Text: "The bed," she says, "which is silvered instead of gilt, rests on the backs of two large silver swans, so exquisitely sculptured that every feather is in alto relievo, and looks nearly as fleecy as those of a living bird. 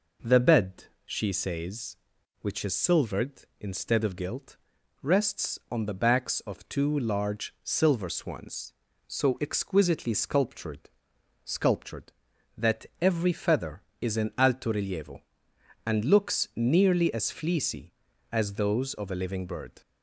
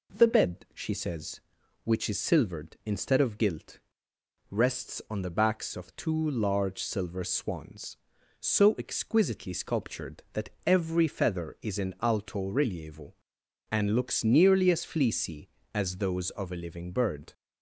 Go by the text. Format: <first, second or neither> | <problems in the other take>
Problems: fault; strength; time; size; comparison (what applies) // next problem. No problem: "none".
second | says "sculptured" twice; at 11.4 s // pauses between "that" and "every"; slight; at 12.8 s; 0.16 s long; slight in the second